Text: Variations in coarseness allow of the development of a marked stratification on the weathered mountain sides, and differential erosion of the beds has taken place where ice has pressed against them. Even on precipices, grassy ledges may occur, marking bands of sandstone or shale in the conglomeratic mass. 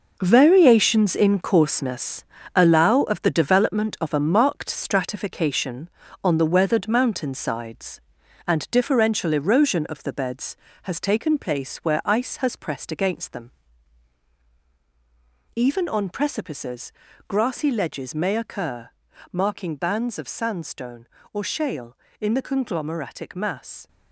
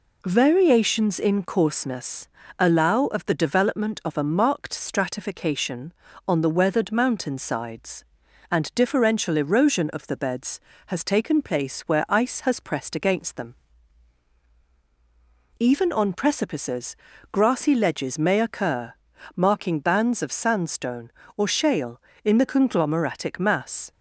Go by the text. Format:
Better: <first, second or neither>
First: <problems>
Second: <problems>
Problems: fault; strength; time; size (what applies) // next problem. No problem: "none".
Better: second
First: gets quieter; strong; throughout; 10 dB // pauses between "coarseness" and "allow"; slight; at 2.2 s; 0.32 s long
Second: pauses between "coarseness" and "allow"; slight; at 2.2 s; 0.32 s long